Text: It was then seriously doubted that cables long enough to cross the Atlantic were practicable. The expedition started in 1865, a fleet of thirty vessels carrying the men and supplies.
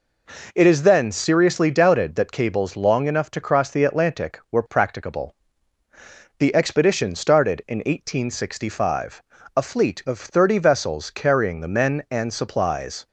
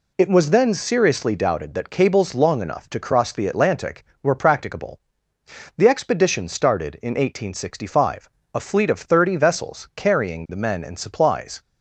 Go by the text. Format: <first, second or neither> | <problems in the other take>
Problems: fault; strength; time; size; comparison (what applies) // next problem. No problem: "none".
second | says "is" for "was"; at 0.6 s